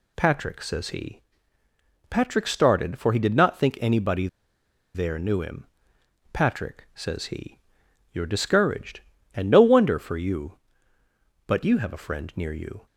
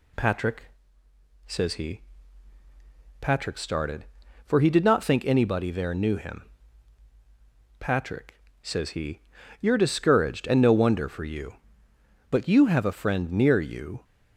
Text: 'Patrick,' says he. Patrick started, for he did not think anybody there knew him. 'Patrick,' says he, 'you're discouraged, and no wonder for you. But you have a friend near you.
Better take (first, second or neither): second